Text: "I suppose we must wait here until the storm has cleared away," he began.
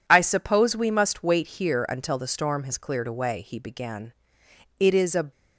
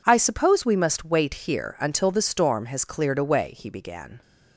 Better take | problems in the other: second | goes on to say "It is a"; from 4.7 s on; 0.52 s long

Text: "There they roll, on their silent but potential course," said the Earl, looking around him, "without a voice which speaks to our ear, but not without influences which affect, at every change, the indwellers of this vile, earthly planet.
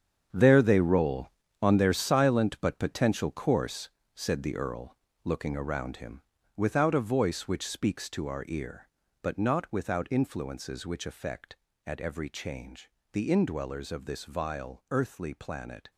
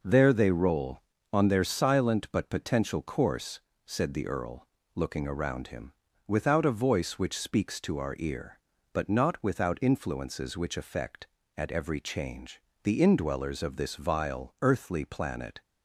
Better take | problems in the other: second | gets quieter; strong; throughout; 12 dB

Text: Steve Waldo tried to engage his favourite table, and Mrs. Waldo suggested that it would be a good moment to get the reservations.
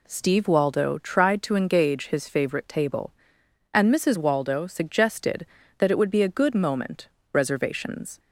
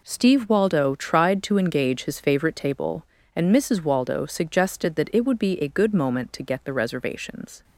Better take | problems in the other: second | skips "to get the"; at 7.1 s

